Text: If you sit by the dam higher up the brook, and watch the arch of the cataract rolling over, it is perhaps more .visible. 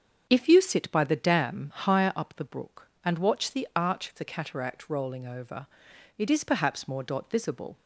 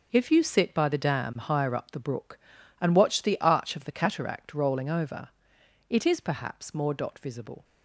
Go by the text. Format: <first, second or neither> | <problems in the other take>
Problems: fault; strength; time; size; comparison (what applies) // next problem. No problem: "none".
neither | starts louder than the rest; the same in both